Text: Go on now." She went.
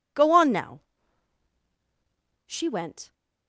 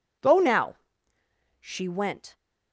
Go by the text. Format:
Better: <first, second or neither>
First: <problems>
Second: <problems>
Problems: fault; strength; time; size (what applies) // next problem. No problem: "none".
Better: first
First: none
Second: skips "on"; at 0.3 s